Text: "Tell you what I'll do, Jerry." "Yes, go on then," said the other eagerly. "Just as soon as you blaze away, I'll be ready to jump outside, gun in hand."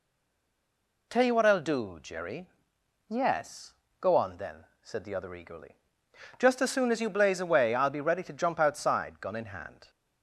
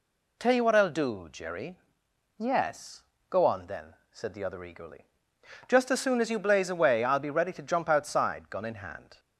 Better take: second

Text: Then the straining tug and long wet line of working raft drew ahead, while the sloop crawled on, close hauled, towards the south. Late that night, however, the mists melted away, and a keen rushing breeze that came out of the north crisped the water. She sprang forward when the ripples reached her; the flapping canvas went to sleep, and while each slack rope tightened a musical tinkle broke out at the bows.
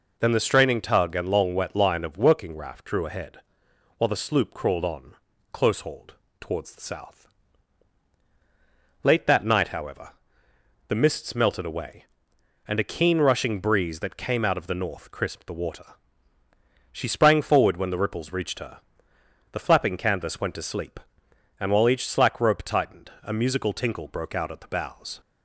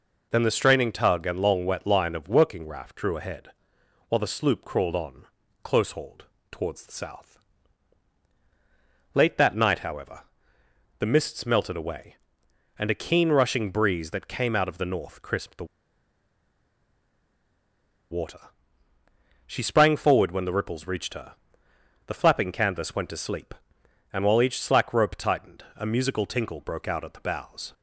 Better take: first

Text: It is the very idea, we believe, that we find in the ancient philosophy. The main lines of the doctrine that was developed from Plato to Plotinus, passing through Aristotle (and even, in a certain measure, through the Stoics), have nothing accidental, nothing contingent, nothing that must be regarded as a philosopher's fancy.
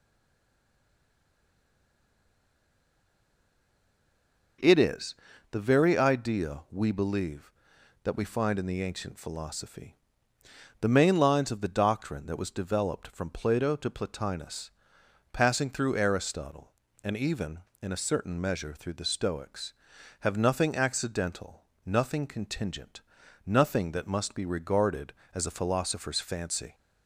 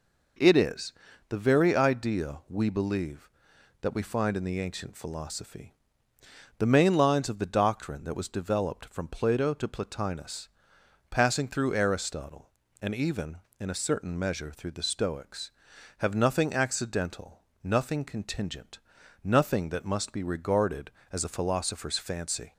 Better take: second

